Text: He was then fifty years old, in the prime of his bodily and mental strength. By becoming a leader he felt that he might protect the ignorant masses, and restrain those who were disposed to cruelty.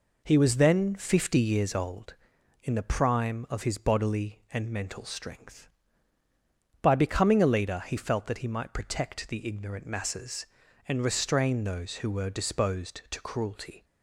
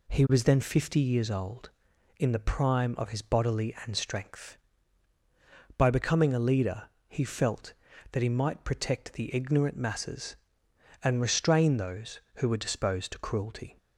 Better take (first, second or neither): first